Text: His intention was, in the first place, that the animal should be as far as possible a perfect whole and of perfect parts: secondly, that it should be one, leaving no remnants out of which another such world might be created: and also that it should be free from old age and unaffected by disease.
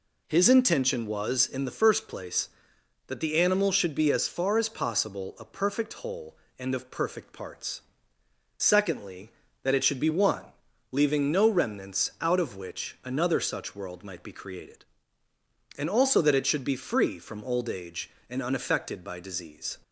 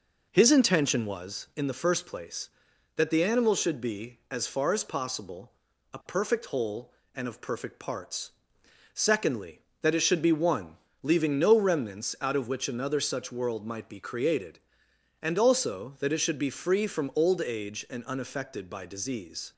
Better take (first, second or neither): first